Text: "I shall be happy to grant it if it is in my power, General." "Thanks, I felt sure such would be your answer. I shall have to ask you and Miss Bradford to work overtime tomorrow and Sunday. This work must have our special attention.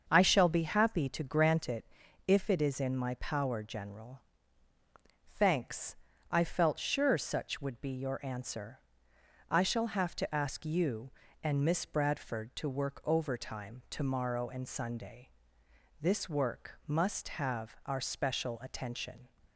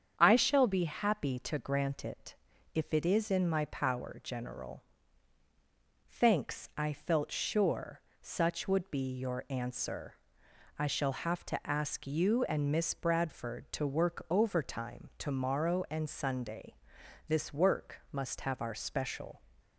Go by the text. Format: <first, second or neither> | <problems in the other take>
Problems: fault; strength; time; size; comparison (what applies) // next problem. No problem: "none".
first | starts louder than the rest; strong; until 1.1 s; 8 dB; also in the first // pauses between "it" and "if"; at 2.3 s; 0.40 s long; also in the first // pauses between "sure" and "such"; slight; at 8.0 s; 0.18 s long // stops before "attention"; at 19.5 s